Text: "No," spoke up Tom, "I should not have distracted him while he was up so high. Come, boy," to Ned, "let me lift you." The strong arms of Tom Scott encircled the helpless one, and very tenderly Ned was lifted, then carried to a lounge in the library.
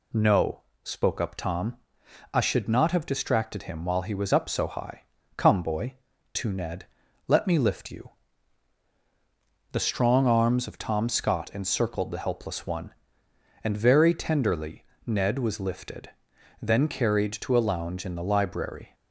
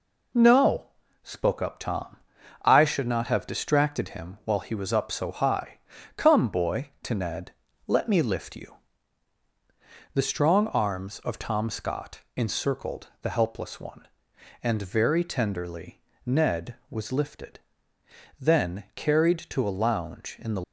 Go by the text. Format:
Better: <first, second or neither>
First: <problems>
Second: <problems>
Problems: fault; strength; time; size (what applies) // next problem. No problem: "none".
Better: first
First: pauses between "tenderly" and "Ned"; slight; at 14.8 s; 0.22 s long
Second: pauses between "Scott" and "encircled"; slight; at 12.1 s; 0.16 s long // pauses between "tenderly" and "Ned"; slight; at 15.9 s; 0.24 s long // stops before "library"; at 20.6 s